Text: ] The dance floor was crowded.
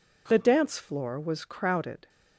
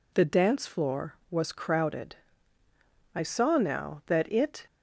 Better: first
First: none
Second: goes on to say "I saw now that it"; from 3.1 s on; 1.5 s long

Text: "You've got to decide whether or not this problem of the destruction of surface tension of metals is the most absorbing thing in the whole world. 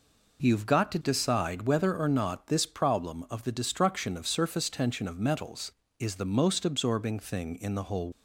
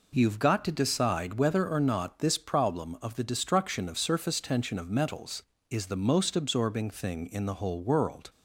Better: second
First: stops before "world"; at 8.1 s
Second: none

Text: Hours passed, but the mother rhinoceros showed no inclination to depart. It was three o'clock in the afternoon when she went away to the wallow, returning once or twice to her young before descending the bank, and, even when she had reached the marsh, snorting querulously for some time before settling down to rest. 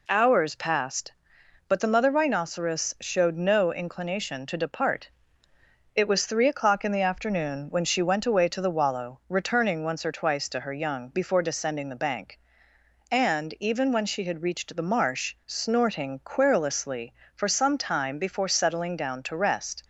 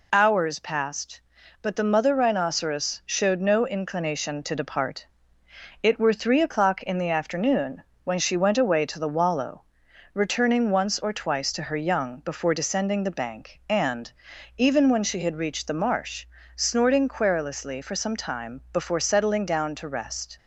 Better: first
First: none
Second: says "were" for "was"; at 5.9 s // pauses between "afternoon" and "when"; slight; at 7.8 s; 0.22 s long

